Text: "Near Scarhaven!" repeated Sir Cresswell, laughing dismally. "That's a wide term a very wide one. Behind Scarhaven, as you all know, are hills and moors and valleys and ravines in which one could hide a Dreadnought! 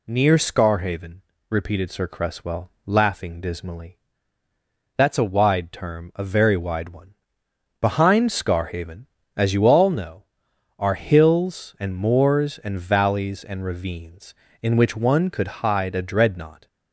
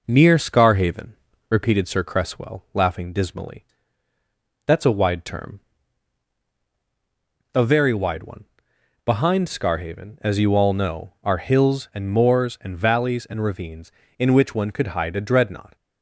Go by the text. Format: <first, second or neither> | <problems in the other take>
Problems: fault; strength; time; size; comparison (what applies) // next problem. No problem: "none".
first | starts louder than the rest; noticeable; until 1.7 s; 5 dB // pauses between "term" and "a"; strong; at 5.6 s; 1.9 s long